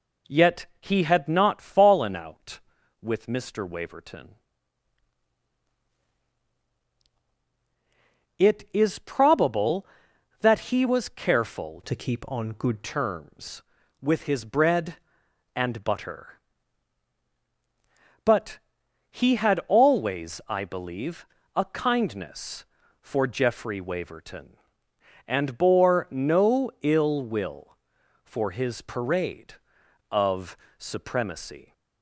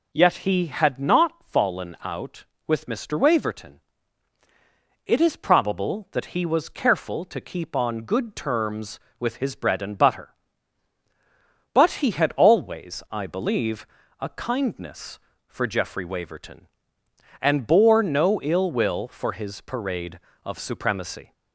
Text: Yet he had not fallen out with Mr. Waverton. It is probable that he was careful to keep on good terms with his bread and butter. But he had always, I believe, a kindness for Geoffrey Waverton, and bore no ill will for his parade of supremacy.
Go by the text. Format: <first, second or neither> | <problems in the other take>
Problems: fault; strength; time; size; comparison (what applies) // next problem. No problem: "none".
second | changes voice from "to" to "good"; from 11.8 to 12.8 s; 1.0 s long // pauses between "But" and "he"; noticeable; at 18.5 s; 0.52 s long // pauses between "of" and "supremacy"; slight; at 30.5 s; 0.20 s long